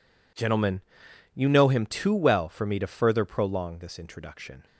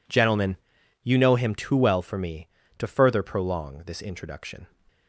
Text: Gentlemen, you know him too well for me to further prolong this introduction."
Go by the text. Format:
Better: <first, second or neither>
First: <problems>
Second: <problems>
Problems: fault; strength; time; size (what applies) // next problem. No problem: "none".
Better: neither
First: none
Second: none